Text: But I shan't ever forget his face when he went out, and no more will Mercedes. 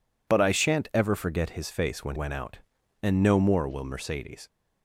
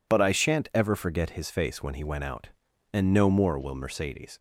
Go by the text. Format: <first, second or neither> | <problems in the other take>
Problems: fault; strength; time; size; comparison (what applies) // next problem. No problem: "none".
second | skips "he"; at 2.1 s